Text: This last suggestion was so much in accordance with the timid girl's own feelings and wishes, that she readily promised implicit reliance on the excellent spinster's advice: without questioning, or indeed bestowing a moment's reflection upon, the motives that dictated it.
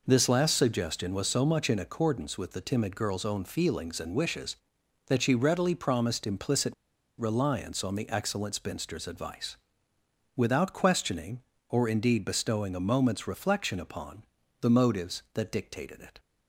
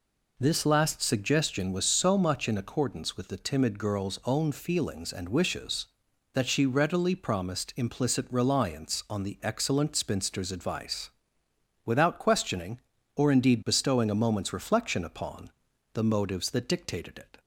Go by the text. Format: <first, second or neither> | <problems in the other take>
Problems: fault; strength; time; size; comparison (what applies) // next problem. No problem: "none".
second | pauses between "implicit" and "reliance"; at 6.7 s; 0.45 s long